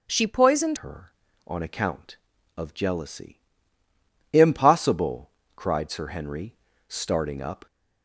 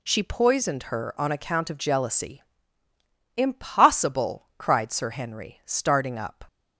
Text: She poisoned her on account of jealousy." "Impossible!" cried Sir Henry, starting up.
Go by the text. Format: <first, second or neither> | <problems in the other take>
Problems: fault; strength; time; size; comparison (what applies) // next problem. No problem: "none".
second | starts louder than the rest; strong; until 1.0 s; 7 dB // changes voice at "her"; from 0.7 s on; 6.9 s long